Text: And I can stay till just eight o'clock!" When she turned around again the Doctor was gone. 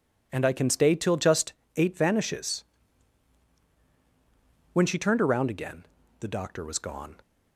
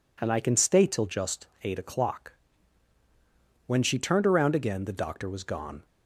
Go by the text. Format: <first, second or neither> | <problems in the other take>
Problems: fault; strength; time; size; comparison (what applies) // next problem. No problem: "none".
second | pauses between "just" and "eight"; slight; at 1.5 s; 0.22 s long; slight in the second // says "vanishes" for "o'clock"; at 1.9 s // pauses between "again" and "the"; slight; at 5.8 s; 0.34 s long